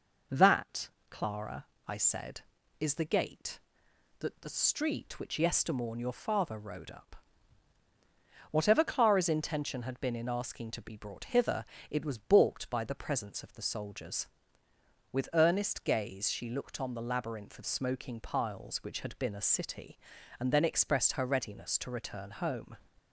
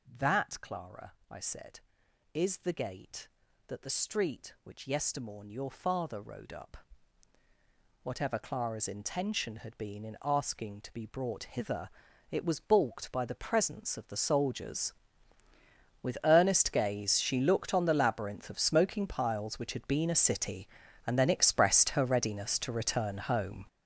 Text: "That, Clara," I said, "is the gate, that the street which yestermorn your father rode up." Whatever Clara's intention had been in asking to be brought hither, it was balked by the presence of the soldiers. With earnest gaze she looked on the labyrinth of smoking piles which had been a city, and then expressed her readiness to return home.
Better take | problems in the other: first | gets louder; strong; throughout; 12 dB

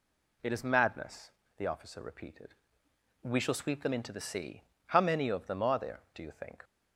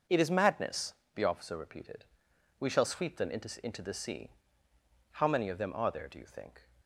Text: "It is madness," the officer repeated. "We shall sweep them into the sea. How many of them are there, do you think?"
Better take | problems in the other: first | starts louder than the rest; until 1.3 s; 6 dB // says "into" twice; at 3.6 s

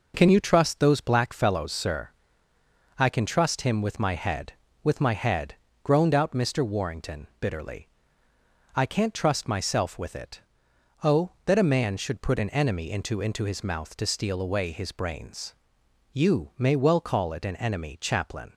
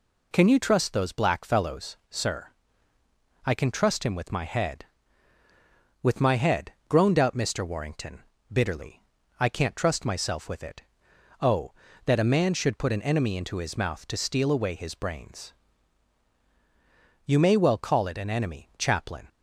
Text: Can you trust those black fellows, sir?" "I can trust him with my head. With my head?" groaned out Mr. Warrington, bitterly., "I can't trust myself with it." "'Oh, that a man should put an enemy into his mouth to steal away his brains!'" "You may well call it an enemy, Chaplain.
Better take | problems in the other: second | says "into" twice; at 13.1 s

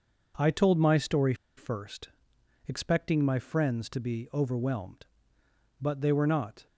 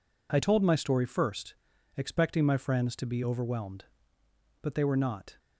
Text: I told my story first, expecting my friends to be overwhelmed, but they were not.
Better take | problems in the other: second | pauses between "story" and "first"; slight; at 1.3 s; 0.23 s long

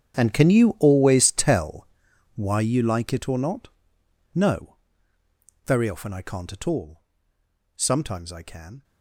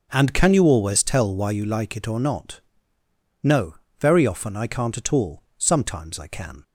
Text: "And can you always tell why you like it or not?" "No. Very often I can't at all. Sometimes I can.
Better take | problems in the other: second | gets quieter; strong; throughout; 17.5 dB // pauses between "tell" and "why"; noticeable; at 1.8 s; 0.48 s long

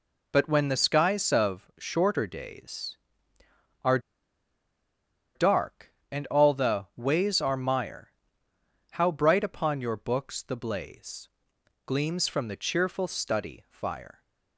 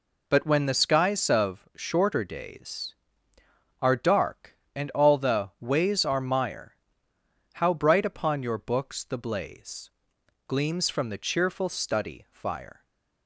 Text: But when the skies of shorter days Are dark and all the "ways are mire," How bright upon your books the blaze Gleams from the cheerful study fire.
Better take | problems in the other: second | pauses between "Are" and "dark"; strong; at 3.9 s; 1.3 s long // pauses between "blaze" and "Gleams"; noticeable; at 11.2 s; 0.58 s long; noticeable in the second

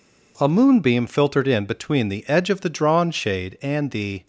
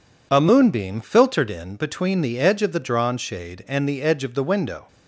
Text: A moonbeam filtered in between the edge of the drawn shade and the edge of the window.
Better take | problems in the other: second | stops before "edge of the window"; at 4.2 s

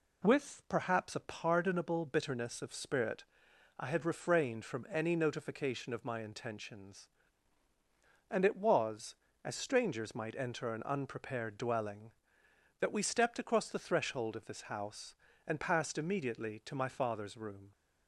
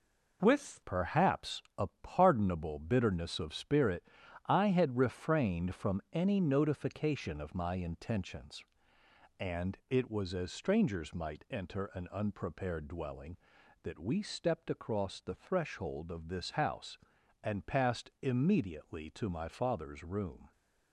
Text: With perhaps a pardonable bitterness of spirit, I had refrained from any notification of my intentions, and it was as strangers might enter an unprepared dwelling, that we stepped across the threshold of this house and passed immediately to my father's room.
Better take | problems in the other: first | changes voice at "perhaps"; from 0.8 s on; 19.7 s long

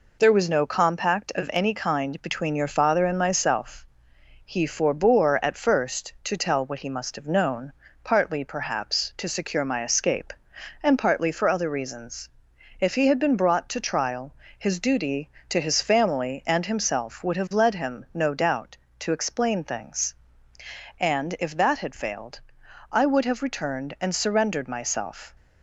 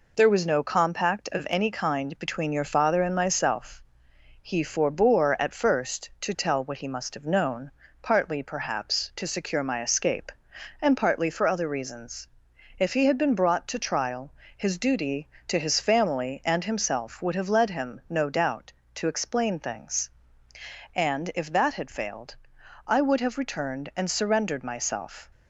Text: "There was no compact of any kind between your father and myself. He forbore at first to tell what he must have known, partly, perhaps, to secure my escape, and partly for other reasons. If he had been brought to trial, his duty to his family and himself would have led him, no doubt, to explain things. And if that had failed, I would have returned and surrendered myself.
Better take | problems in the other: neither | none

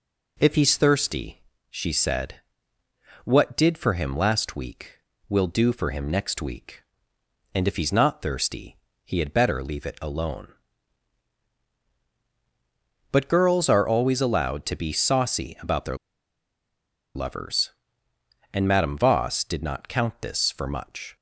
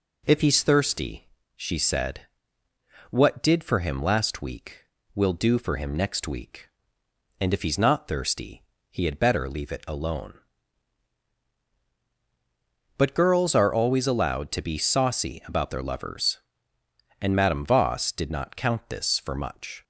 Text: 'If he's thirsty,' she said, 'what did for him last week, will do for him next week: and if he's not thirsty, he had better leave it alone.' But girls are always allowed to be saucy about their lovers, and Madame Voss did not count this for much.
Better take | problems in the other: second | pauses between "their" and "lovers"; at 15.9 s; 1.1 s long

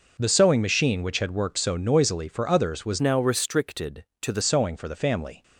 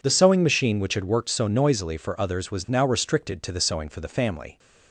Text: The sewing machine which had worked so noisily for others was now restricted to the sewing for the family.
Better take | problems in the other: second | changes voice from "now" to "the"; from 2.9 to 4.4 s; 1.5 s long

